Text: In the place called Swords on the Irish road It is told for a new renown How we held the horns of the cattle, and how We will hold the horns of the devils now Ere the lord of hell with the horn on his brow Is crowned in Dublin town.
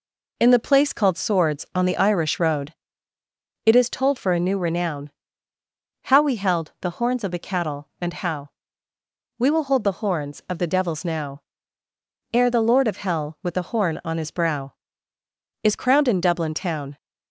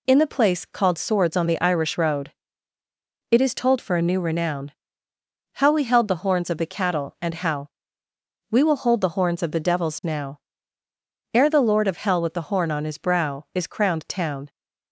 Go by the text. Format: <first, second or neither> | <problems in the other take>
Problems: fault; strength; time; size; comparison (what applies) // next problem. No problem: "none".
first | pauses between "road" and "It"; at 2.3 s; 1.0 s long; noticeable in the first // pauses between "renown" and "How"; noticeable; at 4.6 s; 0.84 s long; noticeable in the first // pauses between "how" and "We"; noticeable; at 7.6 s; 0.82 s long; noticeable in the first // pauses between "now" and "Ere"; noticeable; at 10.3 s; 0.92 s long; noticeable in the first // skips "in Dublin"; at 14.0 s